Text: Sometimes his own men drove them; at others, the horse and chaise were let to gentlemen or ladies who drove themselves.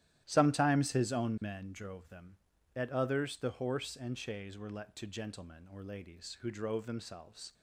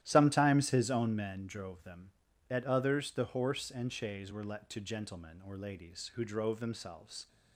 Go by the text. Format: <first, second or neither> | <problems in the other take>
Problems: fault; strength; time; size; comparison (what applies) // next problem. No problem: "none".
neither | starts louder than the rest; strong; the same in both